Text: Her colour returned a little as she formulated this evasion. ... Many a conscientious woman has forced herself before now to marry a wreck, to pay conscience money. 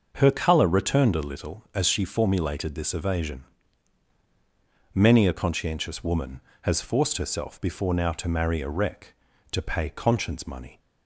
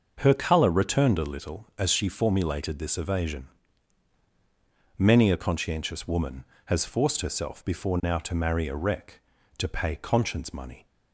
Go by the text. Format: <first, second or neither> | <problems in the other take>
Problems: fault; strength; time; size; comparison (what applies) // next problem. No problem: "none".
neither | starts louder than the rest; the same in both